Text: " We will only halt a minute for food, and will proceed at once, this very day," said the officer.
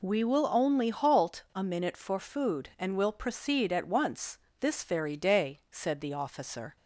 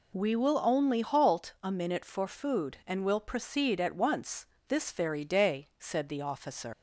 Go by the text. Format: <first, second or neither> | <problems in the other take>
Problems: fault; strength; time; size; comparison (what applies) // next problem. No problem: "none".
first | leaves "officer" unfinished; at 6.7 s; 105 ms